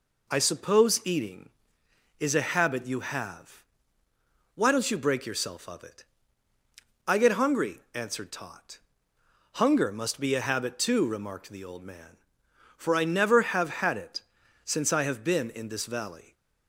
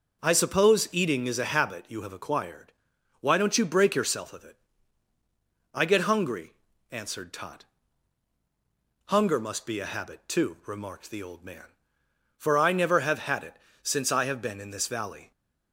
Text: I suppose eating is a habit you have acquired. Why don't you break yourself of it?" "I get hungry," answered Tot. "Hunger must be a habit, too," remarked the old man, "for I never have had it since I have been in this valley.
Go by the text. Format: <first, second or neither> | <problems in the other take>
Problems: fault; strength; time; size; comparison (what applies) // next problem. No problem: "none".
second | skips "acquired"; at 4.0 s // pauses between "it" and "since"; noticeable; at 14.1 s; 0.46 s long; slight in the second